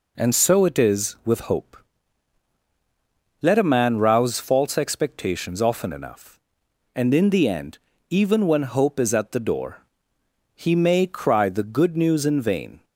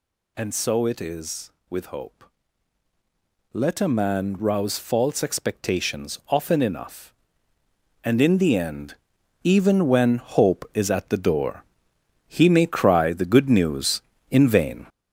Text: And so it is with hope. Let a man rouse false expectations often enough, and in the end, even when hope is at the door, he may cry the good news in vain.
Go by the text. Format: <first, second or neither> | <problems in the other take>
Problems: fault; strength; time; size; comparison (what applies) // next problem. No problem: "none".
first | gets louder; noticeable; throughout; 5.5 dB